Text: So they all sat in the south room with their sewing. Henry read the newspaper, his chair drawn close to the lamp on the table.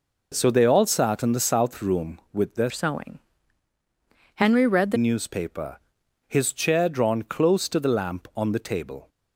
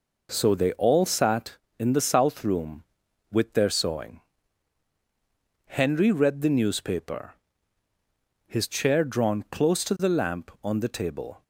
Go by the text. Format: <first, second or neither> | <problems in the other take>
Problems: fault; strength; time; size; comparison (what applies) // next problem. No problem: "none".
second | changes voice from "sewing" to "the"; from 2.6 to 4.9 s; 2.3 s long